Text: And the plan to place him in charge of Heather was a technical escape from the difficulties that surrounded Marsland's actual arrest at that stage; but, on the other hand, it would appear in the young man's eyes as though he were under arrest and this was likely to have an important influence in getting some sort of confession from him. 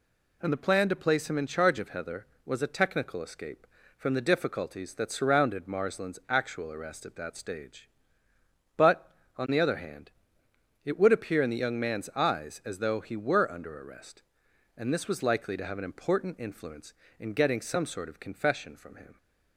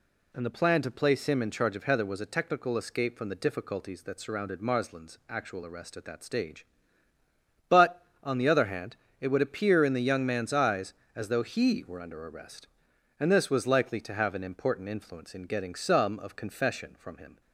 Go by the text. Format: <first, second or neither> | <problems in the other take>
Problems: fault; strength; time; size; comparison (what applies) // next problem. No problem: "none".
first | skips "sort"; at 16.1 s